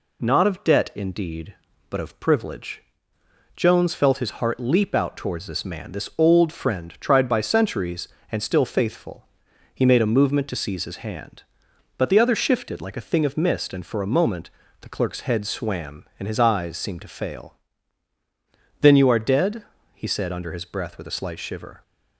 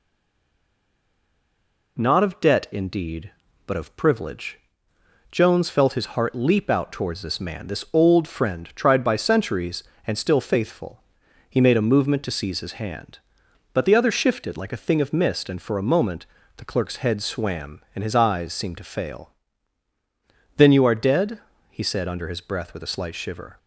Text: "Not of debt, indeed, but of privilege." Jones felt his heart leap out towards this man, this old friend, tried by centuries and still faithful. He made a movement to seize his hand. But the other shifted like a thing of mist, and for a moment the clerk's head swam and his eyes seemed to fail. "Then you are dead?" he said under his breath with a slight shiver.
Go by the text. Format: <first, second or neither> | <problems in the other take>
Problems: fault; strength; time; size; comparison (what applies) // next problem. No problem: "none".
first | stays silent before the first word; noticeable; until 1.9 s; 1.9 s long // pauses between "moment" and "the"; slight; at 16.2 s; 0.32 s long; slight in the first